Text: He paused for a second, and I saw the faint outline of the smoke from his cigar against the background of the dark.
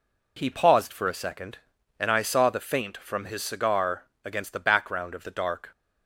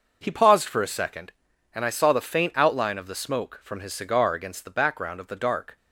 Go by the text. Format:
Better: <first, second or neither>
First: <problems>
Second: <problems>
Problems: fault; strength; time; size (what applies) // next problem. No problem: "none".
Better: second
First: skips "outline of the smoke"; at 2.9 s // pauses between "cigar" and "against"; slight; at 4.0 s; 0.20 s long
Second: none